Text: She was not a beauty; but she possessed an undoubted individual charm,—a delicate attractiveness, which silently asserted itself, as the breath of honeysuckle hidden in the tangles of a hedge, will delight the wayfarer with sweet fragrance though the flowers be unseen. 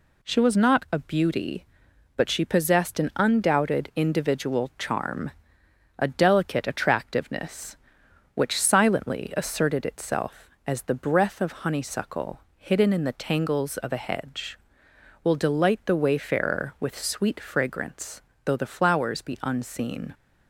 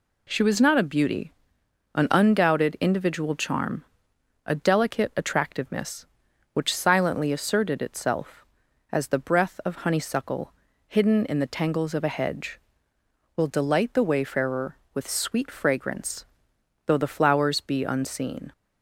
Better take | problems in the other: first | skips "but she possessed"; at 1.6 s // pauses between "honeysuckle" and "hidden"; slight; at 10.5 s; 0.34 s long; slight in the first // pauses between "fragrance" and "though"; noticeable; at 16.2 s; 0.58 s long; slight in the first

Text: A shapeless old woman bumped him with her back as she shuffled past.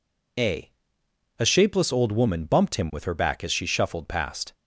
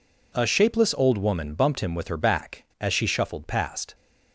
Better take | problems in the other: second | says "A" twice; at 1.3 s

